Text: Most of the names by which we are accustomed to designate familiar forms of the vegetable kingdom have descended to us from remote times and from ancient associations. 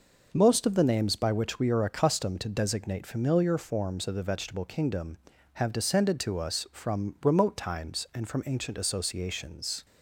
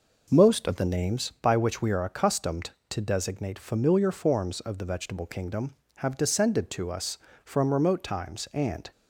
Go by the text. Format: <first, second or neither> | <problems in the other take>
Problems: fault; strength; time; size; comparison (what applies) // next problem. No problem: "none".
first | stops before "from ancient associations"; at 8.9 s